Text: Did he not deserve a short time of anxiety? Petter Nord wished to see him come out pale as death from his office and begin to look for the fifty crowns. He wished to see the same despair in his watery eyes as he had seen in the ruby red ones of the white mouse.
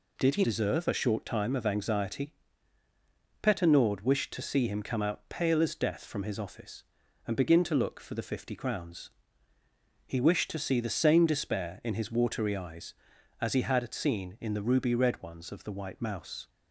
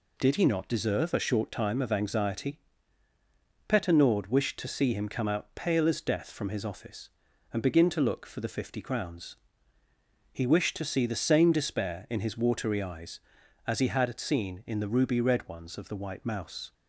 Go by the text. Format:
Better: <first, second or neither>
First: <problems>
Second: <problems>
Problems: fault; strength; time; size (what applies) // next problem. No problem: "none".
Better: second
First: skips "not"; at 0.4 s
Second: none